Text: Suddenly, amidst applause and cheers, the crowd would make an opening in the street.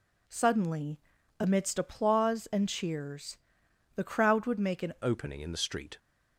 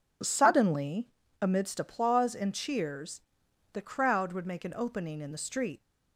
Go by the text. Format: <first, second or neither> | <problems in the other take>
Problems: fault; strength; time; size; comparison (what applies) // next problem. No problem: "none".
second | changes voice at "opening"; from 5.0 s on; 0.9 s long